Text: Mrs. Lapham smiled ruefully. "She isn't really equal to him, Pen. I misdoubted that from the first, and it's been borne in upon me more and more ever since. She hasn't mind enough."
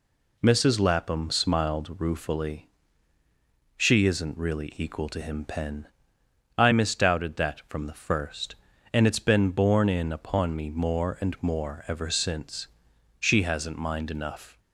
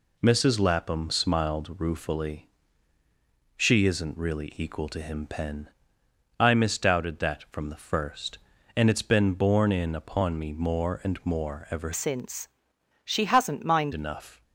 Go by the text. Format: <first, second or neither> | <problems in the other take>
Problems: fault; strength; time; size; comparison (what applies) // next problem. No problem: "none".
first | changes voice from "since" to "mind"; from 11.9 to 13.9 s; 2.0 s long